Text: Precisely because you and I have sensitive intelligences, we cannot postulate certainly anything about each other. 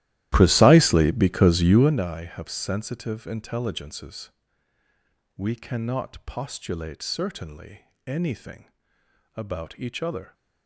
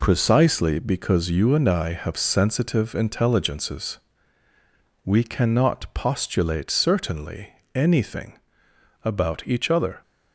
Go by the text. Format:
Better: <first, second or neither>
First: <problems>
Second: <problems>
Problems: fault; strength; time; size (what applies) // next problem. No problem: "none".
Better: second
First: starts louder than the rest; strong; until 2.0 s; 14.5 dB // pauses between "certainly" and "anything"; slight; at 7.8 s; 0.26 s long // pauses between "anything" and "about"; noticeable; at 8.7 s; 0.64 s long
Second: pauses between "certainly" and "anything"; slight; at 7.4 s; 0.26 s long // pauses between "anything" and "about"; noticeable; at 8.3 s; 0.64 s long